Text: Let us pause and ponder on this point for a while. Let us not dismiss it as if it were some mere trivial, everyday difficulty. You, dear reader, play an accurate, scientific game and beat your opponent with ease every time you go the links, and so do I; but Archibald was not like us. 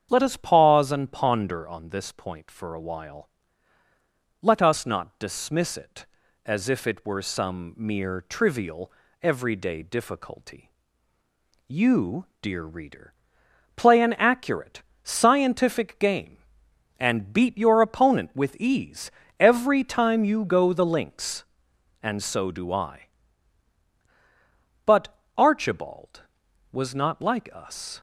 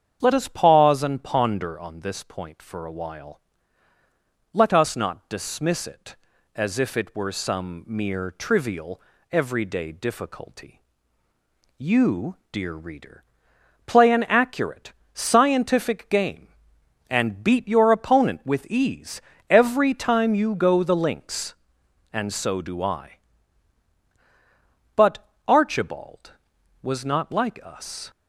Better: neither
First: starts louder than the rest; strong; until 1.1 s; 8 dB // pauses between "ease" and "every"; slight; at 19.0 s; 0.28 s long // pauses between "but" and "Archibald"; slight; at 25.1 s; 0.22 s long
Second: starts louder than the rest; strong; until 1.2 s; 8 dB // pauses between "ease" and "every"; slight; at 19.2 s; 0.28 s long // pauses between "but" and "Archibald"; slight; at 25.2 s; 0.22 s long

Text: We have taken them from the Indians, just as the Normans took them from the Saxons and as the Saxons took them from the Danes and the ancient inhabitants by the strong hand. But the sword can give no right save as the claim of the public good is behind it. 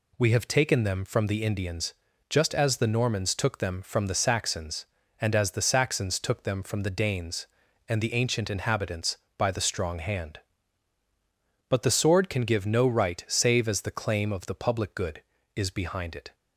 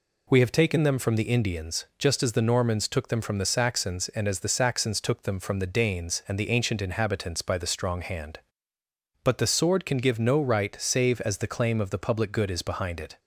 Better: neither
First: none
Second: none

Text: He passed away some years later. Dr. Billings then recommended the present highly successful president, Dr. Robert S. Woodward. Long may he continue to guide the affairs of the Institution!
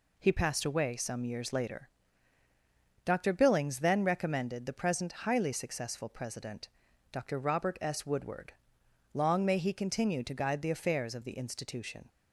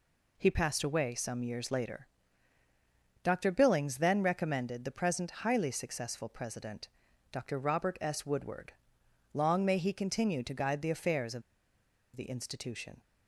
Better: first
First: none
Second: pauses between "of" and "the"; noticeable; at 11.4 s; 0.74 s long

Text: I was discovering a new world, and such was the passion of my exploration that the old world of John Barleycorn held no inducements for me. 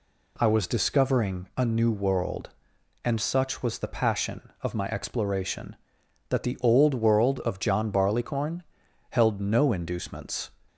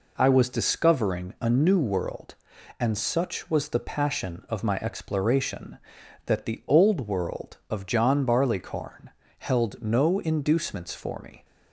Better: second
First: pauses between "Barleycorn" and "held"; noticeable; at 8.6 s; 0.46 s long // stops before "for me"; at 10.6 s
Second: pauses between "Barleycorn" and "held"; slight; at 9.1 s; 0.28 s long

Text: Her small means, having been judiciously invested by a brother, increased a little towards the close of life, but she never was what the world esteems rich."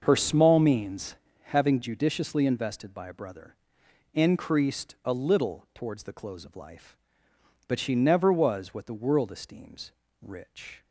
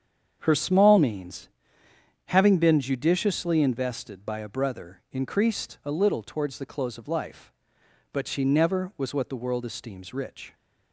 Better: second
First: starts louder than the rest; until 1.0 s; 6.5 dB // skips "been"; at 1.8 s // pauses between "esteems" and "rich"; slight; at 9.9 s; 0.32 s long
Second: starts louder than the rest; strong; until 1.4 s; 8 dB

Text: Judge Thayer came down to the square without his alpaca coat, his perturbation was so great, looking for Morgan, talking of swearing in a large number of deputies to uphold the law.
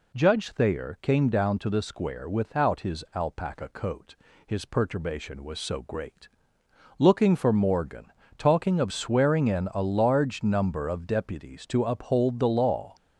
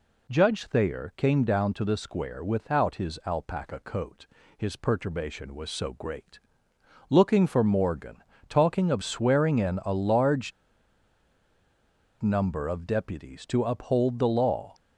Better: first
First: none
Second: pauses between "large" and "number"; strong; at 10.5 s; 1.7 s long

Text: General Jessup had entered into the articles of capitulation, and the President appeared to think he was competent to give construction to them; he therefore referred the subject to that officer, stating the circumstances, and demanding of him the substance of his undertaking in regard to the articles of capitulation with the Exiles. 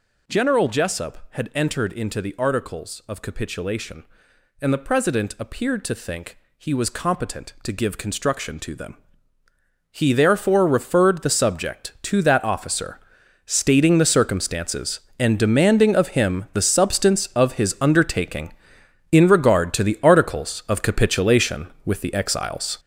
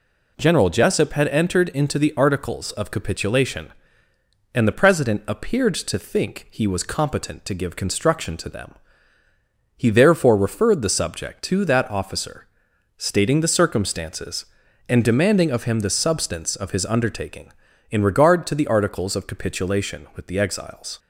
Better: second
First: gets louder; strong; throughout; 9 dB // pauses between "think" and "he"; slight; at 6.3 s; 0.20 s long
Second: none

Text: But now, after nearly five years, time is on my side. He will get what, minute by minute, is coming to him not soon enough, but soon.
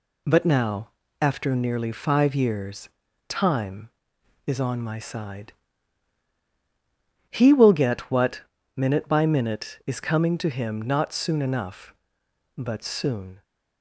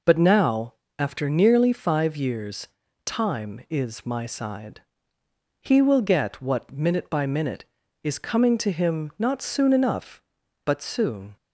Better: first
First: none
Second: skips "on"; at 4.0 s

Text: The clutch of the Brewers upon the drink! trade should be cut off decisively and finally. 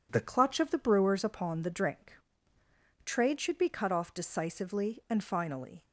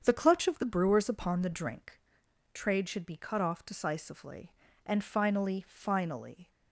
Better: first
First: none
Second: starts louder than the rest; strong; until 1.0 s; 7.5 dB // says "finally" twice; at 5.6 s

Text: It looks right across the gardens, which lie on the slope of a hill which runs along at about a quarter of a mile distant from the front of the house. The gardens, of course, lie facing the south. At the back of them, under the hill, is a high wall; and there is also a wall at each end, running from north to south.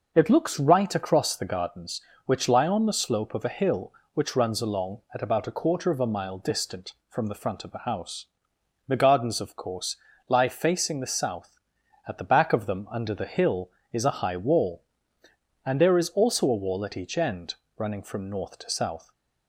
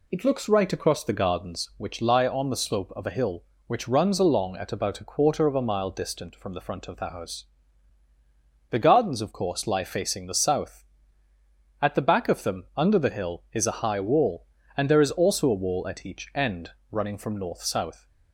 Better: first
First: none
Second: skips "to"; at 17.6 s

